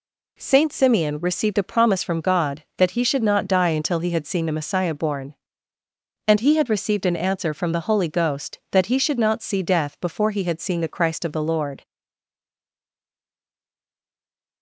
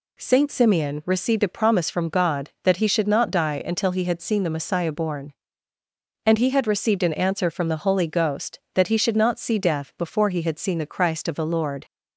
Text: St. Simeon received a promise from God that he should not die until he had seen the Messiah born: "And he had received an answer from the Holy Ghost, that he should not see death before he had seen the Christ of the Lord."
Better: second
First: stays silent after the last word; strong; from 11.8 s on; 2.8 s long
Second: none

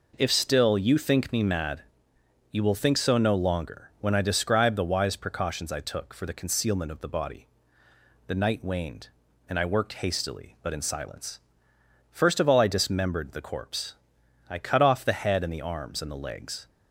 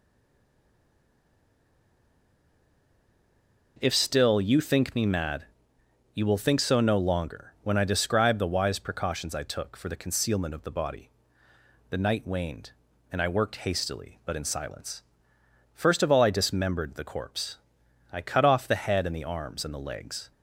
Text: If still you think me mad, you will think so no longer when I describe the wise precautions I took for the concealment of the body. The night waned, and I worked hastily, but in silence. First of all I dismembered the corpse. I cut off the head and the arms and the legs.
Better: first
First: none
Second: stays silent before the first word; strong; until 3.7 s; 3.7 s long

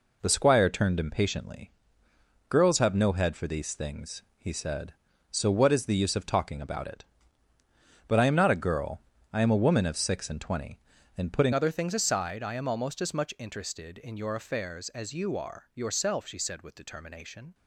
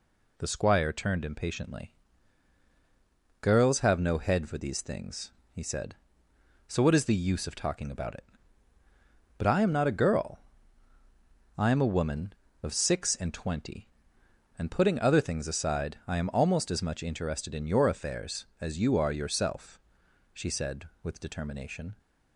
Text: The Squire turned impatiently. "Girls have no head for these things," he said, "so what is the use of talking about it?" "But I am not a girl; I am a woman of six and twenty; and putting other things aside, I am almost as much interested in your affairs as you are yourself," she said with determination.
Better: second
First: changes voice at "other"; from 11.5 s on; 6.0 s long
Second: none

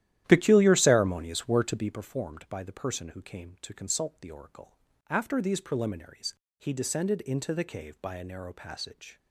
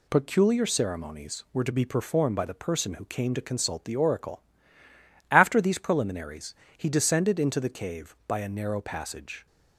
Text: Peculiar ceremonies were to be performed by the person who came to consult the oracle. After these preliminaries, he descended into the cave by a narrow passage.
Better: second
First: starts louder than the rest; strong; until 2.1 s; 12.5 dB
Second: none

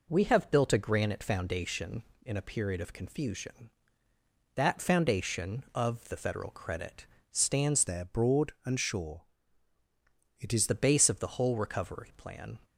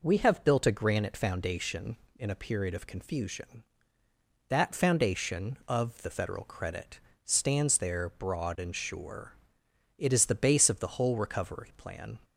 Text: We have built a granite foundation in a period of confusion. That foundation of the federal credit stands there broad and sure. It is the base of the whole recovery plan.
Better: second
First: pauses between "credit" and "stands"; slight; at 7.0 s; 0.26 s long // changes voice from "there" to "is"; from 7.8 to 10.6 s; 2.8 s long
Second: pauses between "credit" and "stands"; slight; at 6.9 s; 0.26 s long

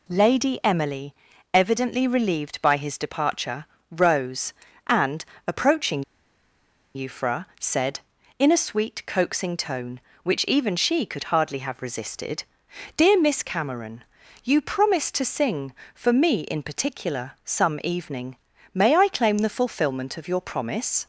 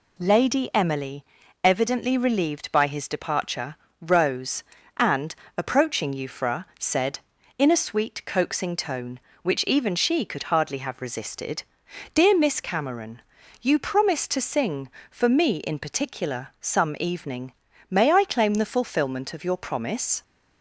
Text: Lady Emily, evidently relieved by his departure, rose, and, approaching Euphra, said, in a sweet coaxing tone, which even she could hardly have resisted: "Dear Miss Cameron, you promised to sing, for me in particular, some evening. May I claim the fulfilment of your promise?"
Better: second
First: pauses between "approaching" and "Euphra"; noticeable; at 6.0 s; 0.93 s long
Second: none

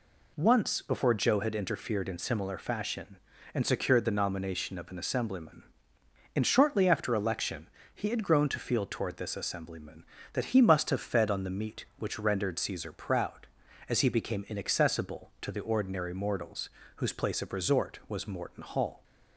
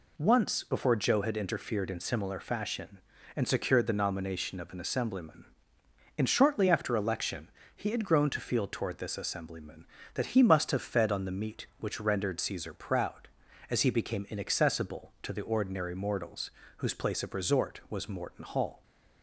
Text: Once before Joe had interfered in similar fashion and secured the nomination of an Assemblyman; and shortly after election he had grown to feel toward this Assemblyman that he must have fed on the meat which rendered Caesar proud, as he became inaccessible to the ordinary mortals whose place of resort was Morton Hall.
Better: neither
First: pauses between "election" and "he"; slight; at 7.6 s; 0.24 s long // pauses between "mortals" and "whose"; slight; at 16.7 s; 0.24 s long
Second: pauses between "election" and "he"; slight; at 7.5 s; 0.24 s long // pauses between "mortals" and "whose"; slight; at 16.5 s; 0.24 s long

